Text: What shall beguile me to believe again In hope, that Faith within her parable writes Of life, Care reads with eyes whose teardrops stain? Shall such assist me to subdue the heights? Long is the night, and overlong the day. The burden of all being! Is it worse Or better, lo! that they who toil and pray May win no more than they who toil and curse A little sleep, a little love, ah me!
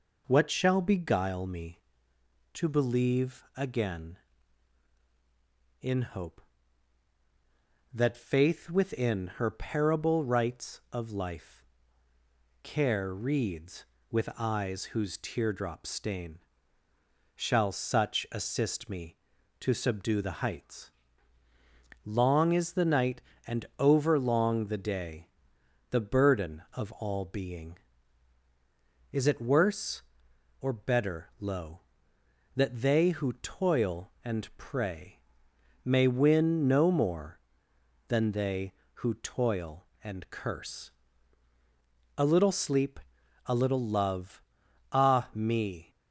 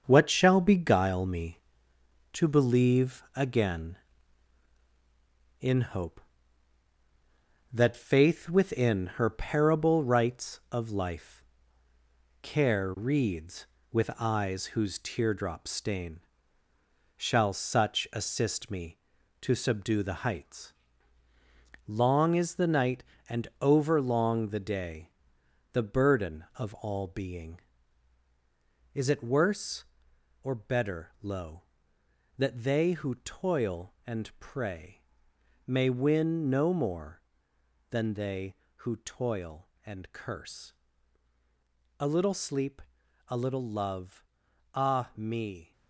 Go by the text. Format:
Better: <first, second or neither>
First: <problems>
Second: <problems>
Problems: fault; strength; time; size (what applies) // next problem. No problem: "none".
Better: first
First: pauses between "pray" and "May"; noticeable; at 35.1 s; 0.66 s long // pauses between "curse" and "A"; at 40.9 s; 1.2 s long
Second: gets quieter; throughout; 6.5 dB // pauses between "pray" and "May"; noticeable; at 34.9 s; 0.66 s long // pauses between "curse" and "A"; at 40.7 s; 1.2 s long